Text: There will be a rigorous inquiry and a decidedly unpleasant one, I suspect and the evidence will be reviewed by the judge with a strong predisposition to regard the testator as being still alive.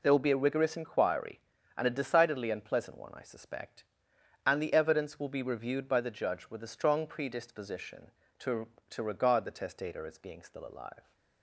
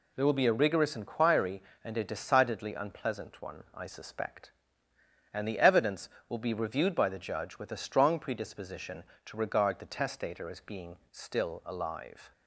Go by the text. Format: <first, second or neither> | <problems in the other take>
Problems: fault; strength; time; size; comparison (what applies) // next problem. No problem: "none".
second | says "to" twice; at 8.9 s